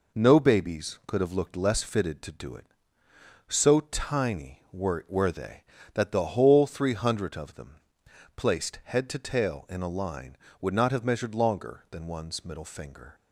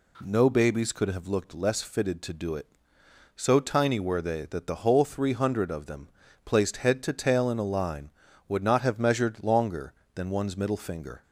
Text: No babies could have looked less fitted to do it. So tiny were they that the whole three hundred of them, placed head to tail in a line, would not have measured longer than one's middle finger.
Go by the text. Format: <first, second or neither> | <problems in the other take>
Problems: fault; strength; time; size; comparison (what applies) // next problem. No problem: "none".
second | says "were" twice; at 5.0 s